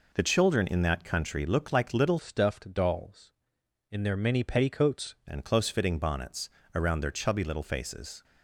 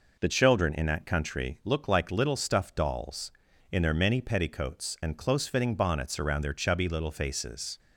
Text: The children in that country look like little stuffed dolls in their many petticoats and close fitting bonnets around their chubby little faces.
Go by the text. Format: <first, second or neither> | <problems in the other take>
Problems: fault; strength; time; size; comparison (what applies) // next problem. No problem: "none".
second | changes voice from "stuffed" to "petticoats"; from 2.1 to 5.1 s; 3.0 s long // pauses between "bonnets" and "around"; slight; at 6.4 s; 0.24 s long